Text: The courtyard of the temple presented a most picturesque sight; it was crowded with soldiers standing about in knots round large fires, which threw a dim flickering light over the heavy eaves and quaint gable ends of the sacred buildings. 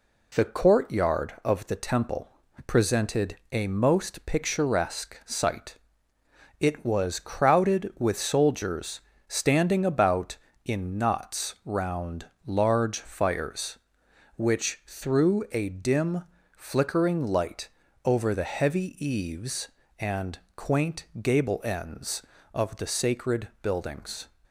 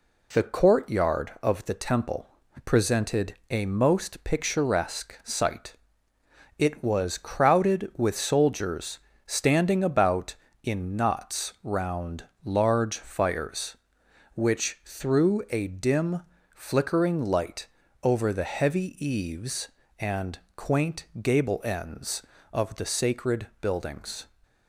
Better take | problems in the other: neither | pauses between "temple" and "presented"; the same in both // pauses between "presented" and "a"; slight; the same in both // pauses between "soldiers" and "standing"; slight; the same in both // pauses between "round" and "large"; slight; the same in both // pauses between "dim" and "flickering"; slight; the same in both // pauses between "light" and "over"; slight; the same in both // pauses between "and" and "quaint"; slight; the same in both

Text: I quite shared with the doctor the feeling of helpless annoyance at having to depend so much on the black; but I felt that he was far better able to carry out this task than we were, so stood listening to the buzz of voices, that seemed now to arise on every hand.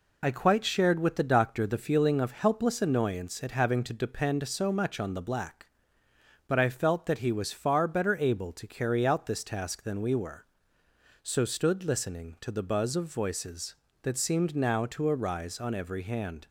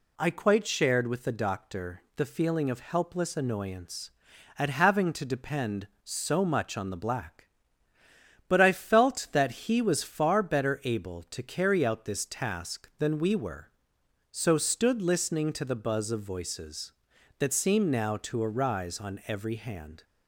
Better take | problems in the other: second | loses the start of "I"; at 0.2 s; 40 ms

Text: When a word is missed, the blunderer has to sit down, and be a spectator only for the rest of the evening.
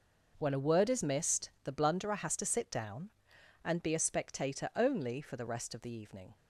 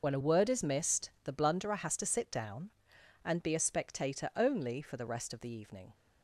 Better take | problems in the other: first | loses the start of "When"; at 0.0 s; 80 ms

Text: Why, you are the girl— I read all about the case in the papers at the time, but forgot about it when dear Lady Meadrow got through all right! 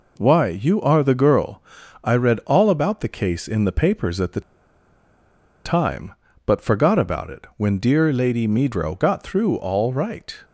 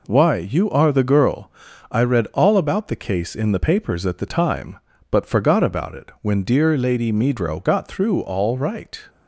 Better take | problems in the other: second | pauses between "the" and "time"; at 4.4 s; 1.2 s long

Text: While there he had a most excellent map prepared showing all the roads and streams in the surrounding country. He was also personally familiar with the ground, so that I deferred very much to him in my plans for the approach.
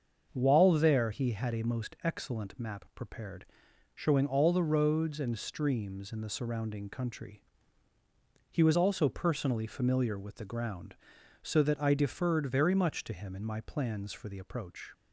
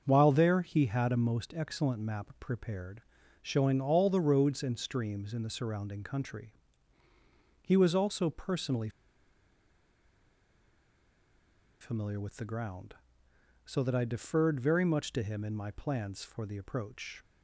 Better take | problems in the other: first | starts louder than the rest; until 1.0 s; 6.5 dB; also in the first // pauses between "prepared" and "showing"; at 3.0 s; 0.38 s long; noticeable in the first // pauses between "personally" and "familiar"; strong; at 8.8 s; 2.9 s long

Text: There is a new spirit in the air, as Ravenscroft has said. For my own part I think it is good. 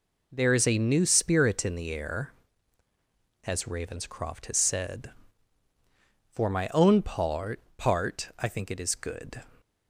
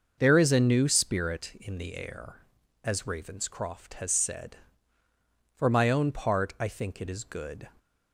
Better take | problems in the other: second | says "part" twice; at 7.7 s

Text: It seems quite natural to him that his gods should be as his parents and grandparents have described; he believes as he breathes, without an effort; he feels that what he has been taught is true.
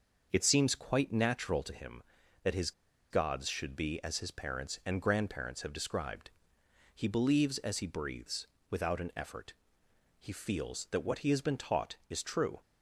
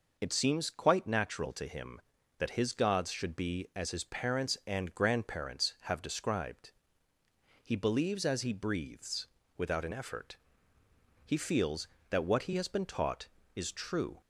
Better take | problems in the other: second | starts louder than the rest; until 1.3 s; 6.5 dB // pauses between "his" and "gods"; at 2.7 s; 0.39 s long

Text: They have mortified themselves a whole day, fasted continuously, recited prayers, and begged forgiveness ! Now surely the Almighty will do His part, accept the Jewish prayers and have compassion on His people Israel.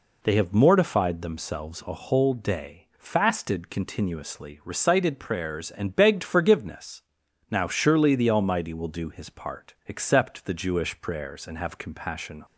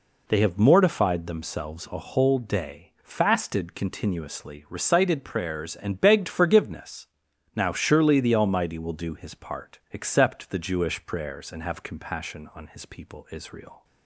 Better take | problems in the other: second | stops before "on His people Israel"; at 12.4 s

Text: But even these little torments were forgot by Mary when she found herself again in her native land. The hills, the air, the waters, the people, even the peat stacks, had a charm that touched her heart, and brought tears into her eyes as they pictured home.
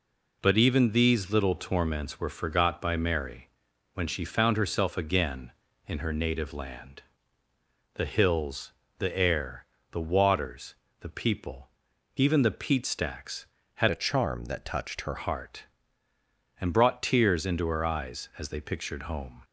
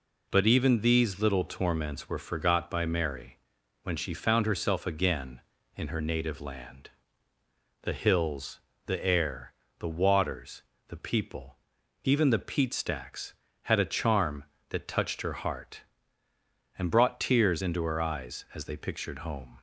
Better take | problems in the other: second | pauses between "Mary" and "when"; noticeable; at 3.4 s; 0.46 s long; noticeable in the second // changes voice from "a" to "her"; from 13.8 to 15.1 s; 1.3 s long

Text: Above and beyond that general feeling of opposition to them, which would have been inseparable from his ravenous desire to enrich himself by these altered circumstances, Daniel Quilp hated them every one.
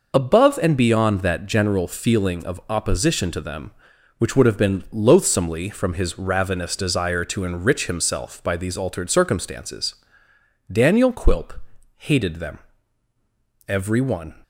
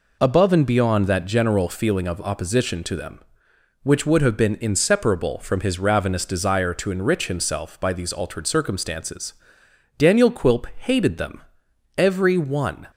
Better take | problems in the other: second | says "loathsomely" for "inseparable"; at 4.9 s // pauses between "Quilp" and "hated"; at 11.5 s; 0.44 s long // pauses between "them" and "every"; at 12.5 s; 1.1 s long; noticeable in the second

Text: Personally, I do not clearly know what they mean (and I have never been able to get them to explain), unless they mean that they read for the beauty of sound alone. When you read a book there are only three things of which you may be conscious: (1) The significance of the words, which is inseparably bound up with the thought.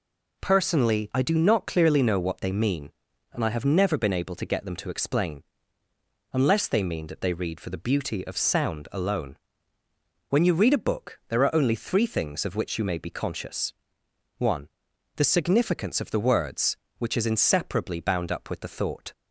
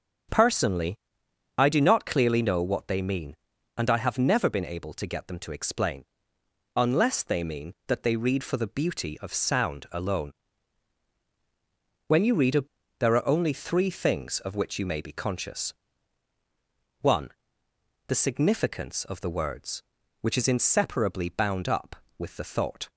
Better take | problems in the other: first | starts louder than the rest; strong; until 1.9 s; 7.5 dB // skips "book"; at 12.8 s

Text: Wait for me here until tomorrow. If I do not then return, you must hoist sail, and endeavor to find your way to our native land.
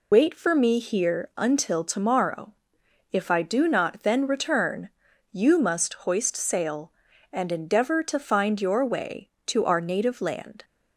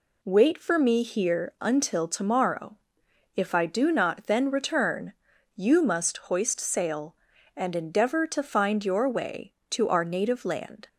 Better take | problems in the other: second | loses the start of "Wait"; at 0.1 s; 120 ms

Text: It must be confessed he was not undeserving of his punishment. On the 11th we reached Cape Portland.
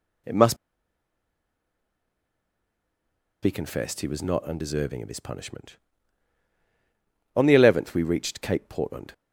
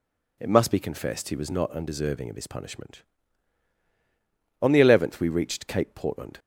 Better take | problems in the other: second | pauses between "must" and "be"; strong; at 0.5 s; 2.8 s long

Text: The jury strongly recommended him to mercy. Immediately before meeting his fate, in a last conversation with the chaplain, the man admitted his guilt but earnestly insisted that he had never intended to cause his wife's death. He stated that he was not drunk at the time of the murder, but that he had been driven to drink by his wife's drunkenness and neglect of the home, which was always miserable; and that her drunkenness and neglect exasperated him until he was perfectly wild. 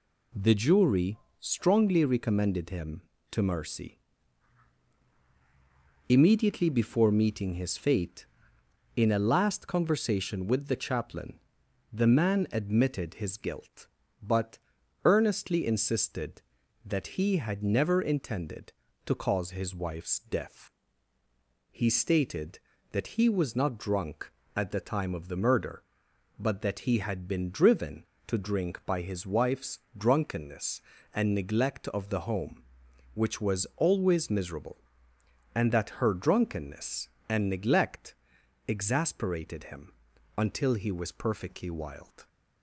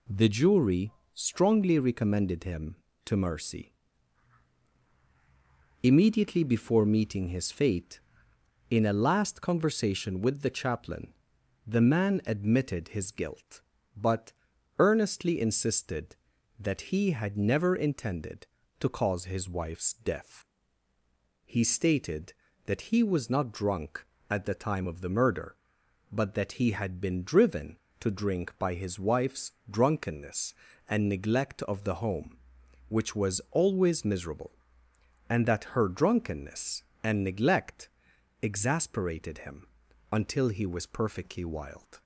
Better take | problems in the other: neither | pauses between "jury" and "strongly"; slight; the same in both // pauses between "but" and "earnestly"; noticeable; the same in both // pauses between "wife's" and "drunkenness"; slight; the same in both // pauses between "neglect" and "exasperated"; noticeable; the same in both // pauses between "him" and "until"; noticeable; the same in both

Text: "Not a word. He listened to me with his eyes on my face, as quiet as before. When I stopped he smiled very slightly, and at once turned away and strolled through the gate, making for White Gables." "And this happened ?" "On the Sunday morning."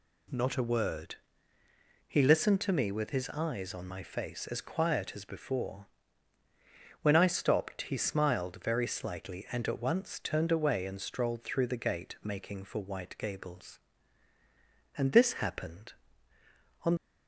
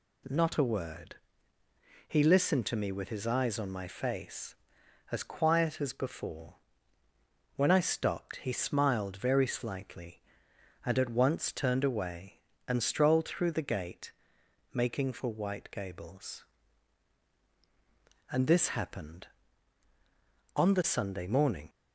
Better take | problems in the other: second | stops before "the Sunday morning"; at 16.9 s

